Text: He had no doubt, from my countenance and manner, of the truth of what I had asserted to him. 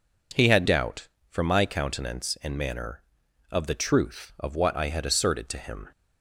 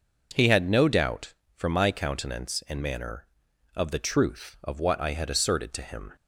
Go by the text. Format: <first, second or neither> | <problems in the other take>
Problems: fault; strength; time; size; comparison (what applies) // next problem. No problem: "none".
second | skips "no"; at 0.6 s